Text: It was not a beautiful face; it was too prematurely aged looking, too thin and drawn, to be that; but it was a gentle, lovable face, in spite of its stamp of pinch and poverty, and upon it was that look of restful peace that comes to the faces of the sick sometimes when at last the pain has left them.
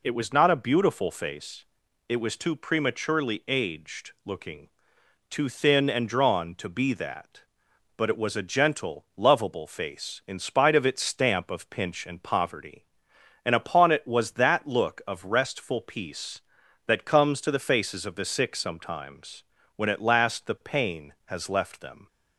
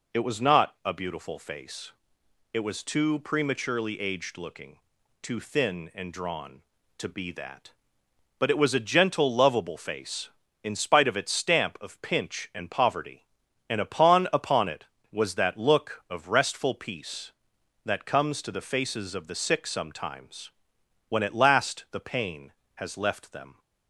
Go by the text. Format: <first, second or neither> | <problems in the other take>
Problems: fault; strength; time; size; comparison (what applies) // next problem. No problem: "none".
first | says "upon" twice; at 14.3 s // pauses between "sometimes" and "when"; noticeable; at 20.5 s; 0.58 s long; slight in the first